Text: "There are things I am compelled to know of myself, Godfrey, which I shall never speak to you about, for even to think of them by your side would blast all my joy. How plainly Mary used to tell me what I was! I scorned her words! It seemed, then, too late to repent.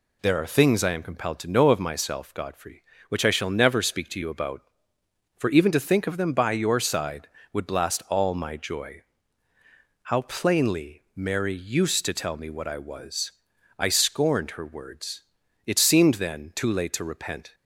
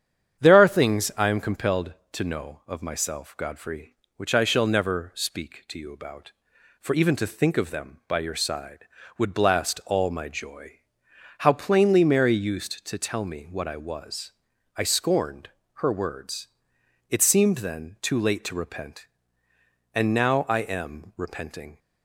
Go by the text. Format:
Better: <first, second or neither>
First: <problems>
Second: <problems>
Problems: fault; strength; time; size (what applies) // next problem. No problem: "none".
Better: first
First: none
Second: starts louder than the rest; strong; until 1.4 s; 8.5 dB // pauses between "scorned" and "her"; slight; at 15.4 s; 0.28 s long // goes on to say "And now I am repenting"; strong; from 19.9 s on; 1.8 s long